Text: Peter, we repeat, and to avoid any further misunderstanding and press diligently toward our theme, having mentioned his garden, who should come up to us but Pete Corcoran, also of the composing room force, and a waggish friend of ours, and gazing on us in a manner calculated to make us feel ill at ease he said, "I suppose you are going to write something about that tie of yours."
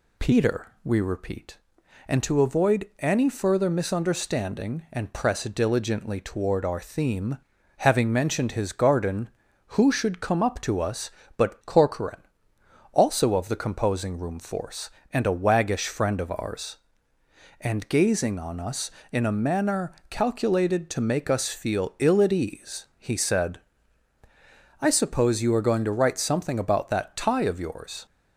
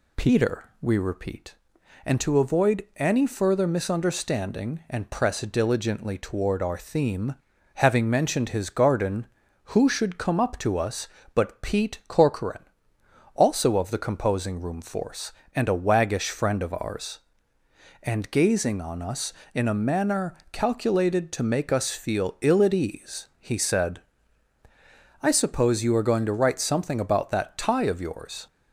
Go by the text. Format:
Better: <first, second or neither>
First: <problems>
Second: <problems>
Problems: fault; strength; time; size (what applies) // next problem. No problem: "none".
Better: second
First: skips "Pete"; at 11.6 s // pauses between "manner" and "calculated"; slight; at 19.9 s; 0.16 s long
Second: pauses between "manner" and "calculated"; slight; at 20.3 s; 0.16 s long